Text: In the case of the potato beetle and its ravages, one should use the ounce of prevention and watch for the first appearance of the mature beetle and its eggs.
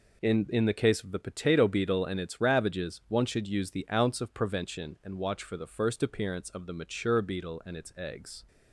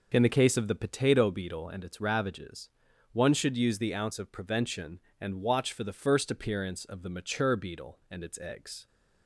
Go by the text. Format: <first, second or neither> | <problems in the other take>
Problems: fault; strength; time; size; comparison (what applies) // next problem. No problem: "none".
second | says "In" twice; at 0.4 s